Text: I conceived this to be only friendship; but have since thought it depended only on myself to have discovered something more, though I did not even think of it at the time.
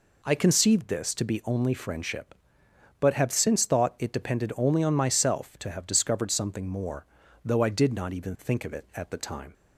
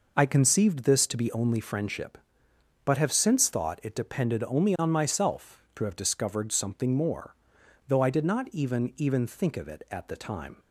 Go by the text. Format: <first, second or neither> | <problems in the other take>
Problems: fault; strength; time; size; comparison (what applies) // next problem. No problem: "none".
first | says "even" twice; at 8.9 s